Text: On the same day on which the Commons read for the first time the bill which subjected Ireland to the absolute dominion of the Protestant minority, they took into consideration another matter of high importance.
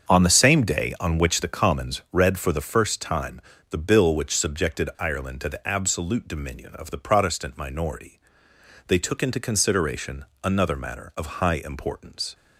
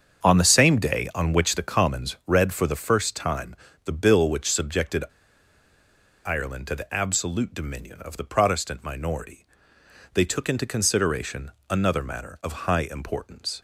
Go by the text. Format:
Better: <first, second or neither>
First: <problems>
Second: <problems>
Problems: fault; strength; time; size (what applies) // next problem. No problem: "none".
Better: first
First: starts louder than the rest; strong; until 1.1 s; 7 dB // pauses between "time" and "the"; slight; at 3.4 s; 0.30 s long // pauses between "consideration" and "another"; slight; at 10.2 s; 0.18 s long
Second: starts louder than the rest; strong; until 1.3 s; 7 dB // pauses between "time" and "the"; slight; at 3.5 s; 0.30 s long // pauses between "subjected" and "Ireland"; at 5.0 s; 1.2 s long // pauses between "consideration" and "another"; slight; at 11.5 s; 0.18 s long